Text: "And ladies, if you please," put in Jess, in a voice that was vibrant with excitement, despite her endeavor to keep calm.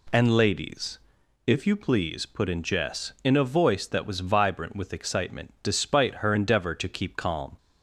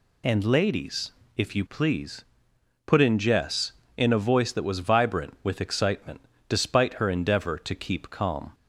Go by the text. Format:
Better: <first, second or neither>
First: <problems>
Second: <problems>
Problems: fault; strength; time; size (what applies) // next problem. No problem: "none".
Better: neither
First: none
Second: none